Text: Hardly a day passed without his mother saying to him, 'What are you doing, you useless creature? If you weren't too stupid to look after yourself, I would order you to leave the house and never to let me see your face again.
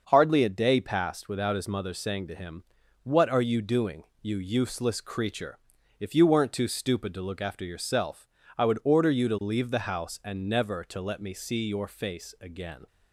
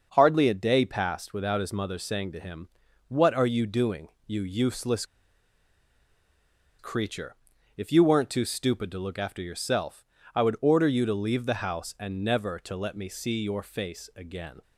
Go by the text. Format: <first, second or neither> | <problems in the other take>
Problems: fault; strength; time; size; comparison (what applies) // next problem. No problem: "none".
first | starts louder than the rest; until 1.1 s; 6 dB; also in the first // pauses between "useless" and "creature"; strong; at 5.0 s; 1.7 s long